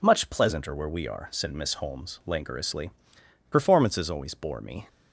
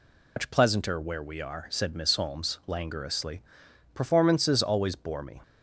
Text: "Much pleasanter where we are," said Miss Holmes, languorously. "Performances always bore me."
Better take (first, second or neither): first